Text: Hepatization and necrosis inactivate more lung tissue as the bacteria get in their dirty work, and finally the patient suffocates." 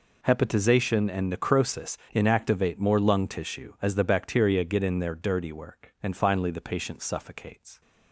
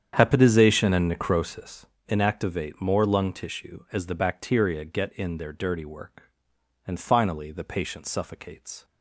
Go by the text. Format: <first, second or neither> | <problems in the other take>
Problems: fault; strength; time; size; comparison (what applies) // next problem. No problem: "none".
first | starts louder than the rest; strong; until 1.9 s; 8.5 dB // pauses between "necrosis" and "inactivate"; slight; at 1.8 s; 0.22 s long; slight in the first